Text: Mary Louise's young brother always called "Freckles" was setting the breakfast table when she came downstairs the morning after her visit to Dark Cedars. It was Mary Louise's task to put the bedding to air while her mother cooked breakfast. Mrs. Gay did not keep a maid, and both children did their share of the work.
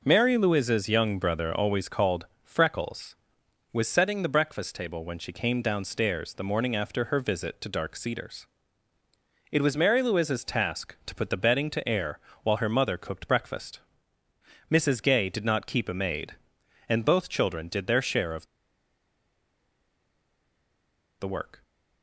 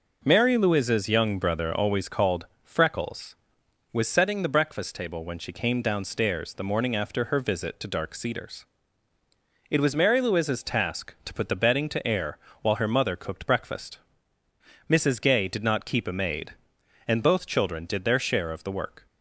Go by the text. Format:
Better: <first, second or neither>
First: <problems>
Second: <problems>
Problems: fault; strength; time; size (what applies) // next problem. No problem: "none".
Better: second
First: pauses between "called" and "Freckles"; slight; at 2.2 s; 0.16 s long // pauses between "air" and "while"; slight; at 12.1 s; 0.24 s long // pauses between "of" and "the"; strong; at 18.4 s; 2.7 s long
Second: pauses between "called" and "Freckles"; slight; at 2.4 s; 0.16 s long // pauses between "air" and "while"; slight; at 12.3 s; 0.24 s long